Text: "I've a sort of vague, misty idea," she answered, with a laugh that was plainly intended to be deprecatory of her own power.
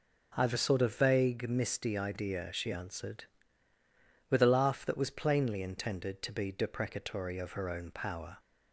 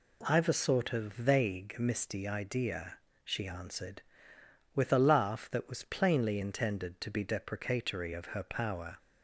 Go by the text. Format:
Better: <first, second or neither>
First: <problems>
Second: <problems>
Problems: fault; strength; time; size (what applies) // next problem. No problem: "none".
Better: first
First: none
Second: skips "own"; at 8.4 s